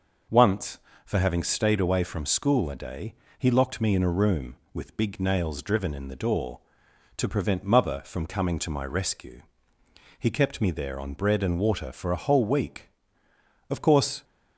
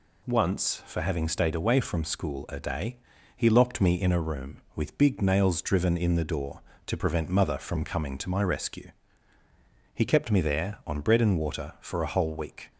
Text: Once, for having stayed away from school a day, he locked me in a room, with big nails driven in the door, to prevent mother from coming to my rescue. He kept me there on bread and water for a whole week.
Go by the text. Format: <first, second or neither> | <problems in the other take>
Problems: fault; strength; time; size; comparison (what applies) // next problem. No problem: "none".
second | goes on to say "Of course"; from 13.6 s on; 0.54 s long